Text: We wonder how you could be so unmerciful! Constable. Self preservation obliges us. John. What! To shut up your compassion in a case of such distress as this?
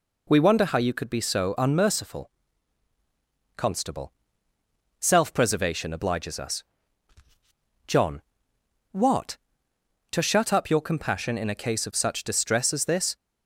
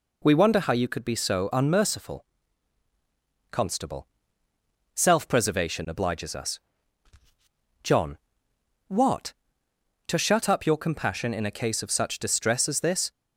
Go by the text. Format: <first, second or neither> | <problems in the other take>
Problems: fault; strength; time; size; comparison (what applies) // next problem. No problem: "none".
neither | none